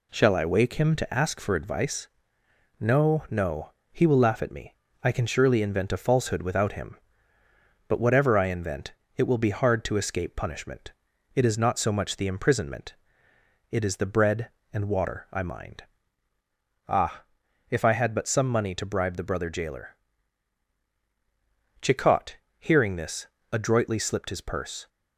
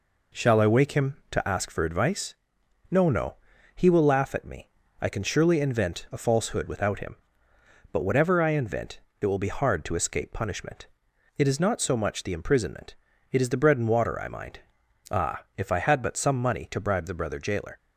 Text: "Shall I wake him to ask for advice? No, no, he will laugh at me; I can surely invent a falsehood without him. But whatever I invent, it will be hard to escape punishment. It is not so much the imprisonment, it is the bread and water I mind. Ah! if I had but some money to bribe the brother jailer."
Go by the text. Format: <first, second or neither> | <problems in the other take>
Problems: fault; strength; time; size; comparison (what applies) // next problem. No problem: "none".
second | goes on to say "Chicot hearing this adroitly slipped his purse"; strong; from 21.8 s on; 3.0 s long